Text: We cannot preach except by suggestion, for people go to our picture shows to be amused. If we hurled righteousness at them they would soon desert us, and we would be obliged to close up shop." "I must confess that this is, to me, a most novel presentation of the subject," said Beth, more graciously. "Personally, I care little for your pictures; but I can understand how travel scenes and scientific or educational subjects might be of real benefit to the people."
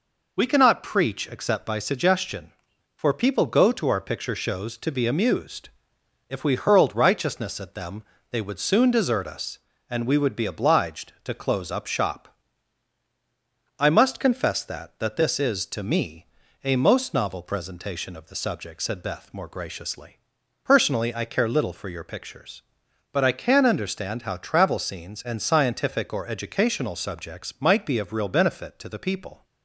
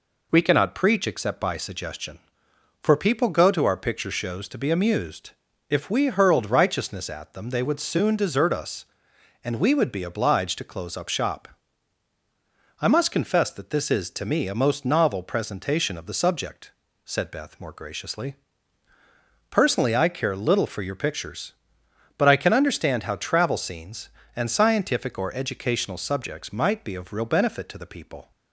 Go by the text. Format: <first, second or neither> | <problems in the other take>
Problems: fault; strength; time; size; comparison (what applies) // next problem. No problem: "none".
second | pauses between "them" and "they"; slight; at 8.0 s; 0.26 s long // says "that" twice; at 14.9 s